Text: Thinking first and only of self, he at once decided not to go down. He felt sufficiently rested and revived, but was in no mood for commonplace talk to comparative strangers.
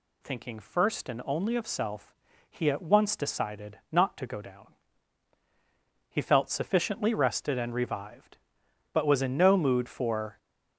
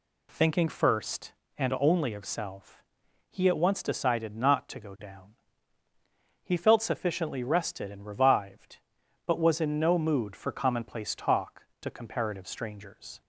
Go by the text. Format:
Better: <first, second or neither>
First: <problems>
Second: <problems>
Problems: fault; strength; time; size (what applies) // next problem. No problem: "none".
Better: second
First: stops before "commonplace talk to comparative strangers"; at 10.3 s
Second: none